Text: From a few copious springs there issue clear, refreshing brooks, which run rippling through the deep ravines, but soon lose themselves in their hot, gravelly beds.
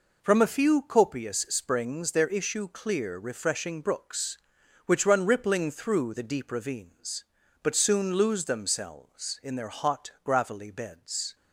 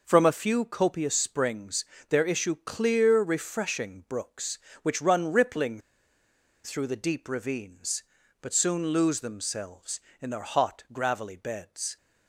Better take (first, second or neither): first